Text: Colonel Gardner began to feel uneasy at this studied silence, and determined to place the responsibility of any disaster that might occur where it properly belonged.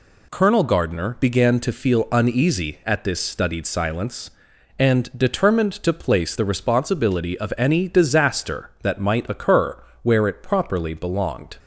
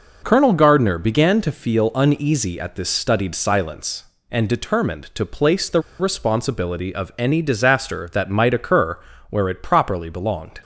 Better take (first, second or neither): first